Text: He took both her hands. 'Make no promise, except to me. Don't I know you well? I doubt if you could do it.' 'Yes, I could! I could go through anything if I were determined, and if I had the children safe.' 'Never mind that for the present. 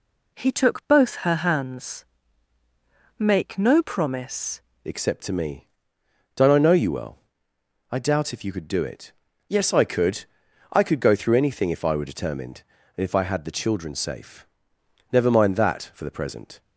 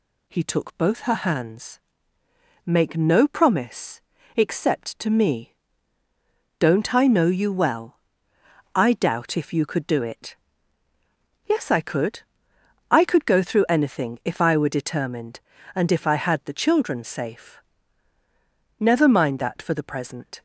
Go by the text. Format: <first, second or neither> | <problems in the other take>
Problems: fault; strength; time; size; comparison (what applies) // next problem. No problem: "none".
second | changes voice at "except"; from 4.8 s on; 11.8 s long